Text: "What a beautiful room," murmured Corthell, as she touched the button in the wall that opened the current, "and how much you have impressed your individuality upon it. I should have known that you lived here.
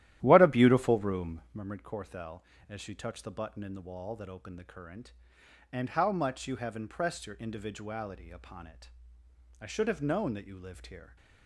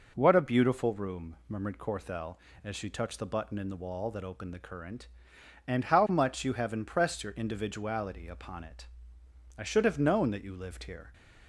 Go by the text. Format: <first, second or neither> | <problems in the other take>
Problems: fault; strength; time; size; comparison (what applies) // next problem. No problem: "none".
second | starts louder than the rest; strong; until 1.6 s; 13 dB